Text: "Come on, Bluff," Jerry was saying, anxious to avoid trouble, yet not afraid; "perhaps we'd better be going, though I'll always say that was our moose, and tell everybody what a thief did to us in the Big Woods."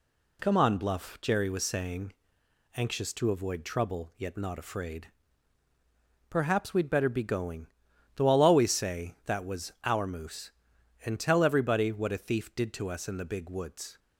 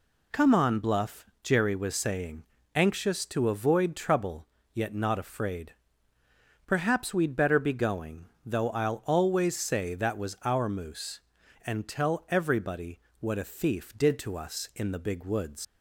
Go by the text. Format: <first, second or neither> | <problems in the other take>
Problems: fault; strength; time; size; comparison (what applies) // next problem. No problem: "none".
first | pauses between "everybody" and "what"; slight; at 13.0 s; 0.18 s long // leaves "Woods" unfinished; at 15.6 s; 115 ms